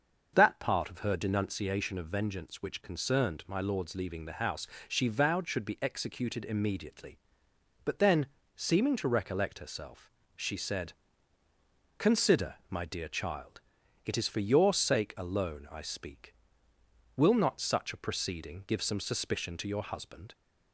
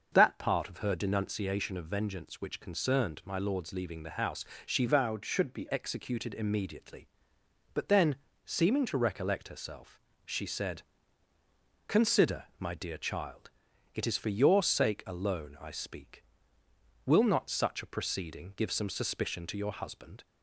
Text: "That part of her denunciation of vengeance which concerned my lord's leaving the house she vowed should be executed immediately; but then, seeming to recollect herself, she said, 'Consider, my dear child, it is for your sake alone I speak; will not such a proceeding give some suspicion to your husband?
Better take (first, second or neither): first